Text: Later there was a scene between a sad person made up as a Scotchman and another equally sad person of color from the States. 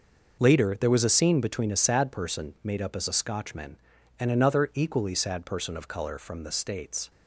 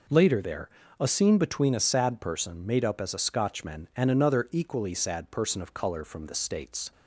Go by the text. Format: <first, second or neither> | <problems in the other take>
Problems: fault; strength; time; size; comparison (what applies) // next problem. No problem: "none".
first | skips "was"; at 0.8 s